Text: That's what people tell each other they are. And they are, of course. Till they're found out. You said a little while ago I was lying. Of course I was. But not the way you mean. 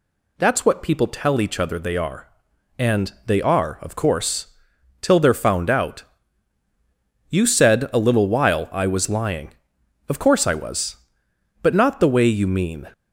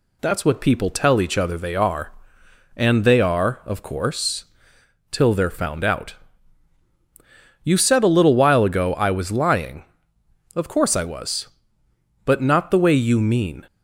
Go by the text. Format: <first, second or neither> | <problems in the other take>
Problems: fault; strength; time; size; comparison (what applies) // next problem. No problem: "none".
second | skips "ago"; at 8.7 s